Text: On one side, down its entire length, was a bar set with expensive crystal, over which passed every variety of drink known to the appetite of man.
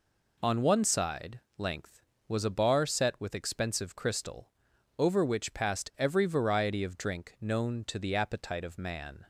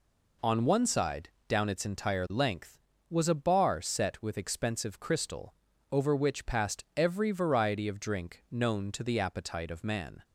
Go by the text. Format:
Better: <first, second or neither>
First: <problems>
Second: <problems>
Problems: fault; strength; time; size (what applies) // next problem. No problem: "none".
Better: second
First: skips "down its entire"; at 1.4 s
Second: none